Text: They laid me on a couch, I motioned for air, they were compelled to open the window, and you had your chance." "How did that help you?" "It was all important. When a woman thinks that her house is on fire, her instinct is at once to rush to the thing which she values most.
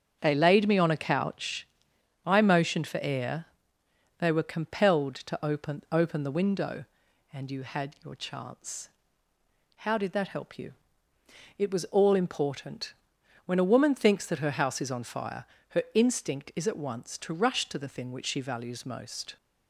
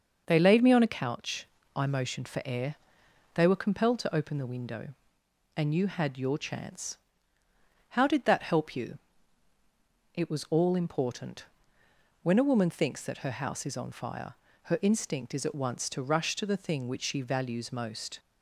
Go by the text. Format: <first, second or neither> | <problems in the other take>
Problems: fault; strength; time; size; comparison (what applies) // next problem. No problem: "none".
second | starts louder than the rest; until 1.2 s; 7 dB; noticeable in the second // says "open" twice; at 5.9 s